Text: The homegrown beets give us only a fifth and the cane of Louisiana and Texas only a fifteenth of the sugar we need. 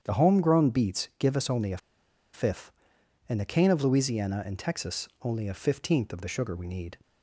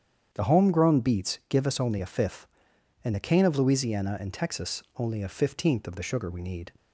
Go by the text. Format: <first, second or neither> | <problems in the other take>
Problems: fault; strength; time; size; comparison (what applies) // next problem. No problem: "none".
second | starts louder than the rest; strong; until 1.0 s; 8.5 dB; strong in the second // pauses between "a" and "fifth"; noticeable; at 1.7 s; 0.56 s long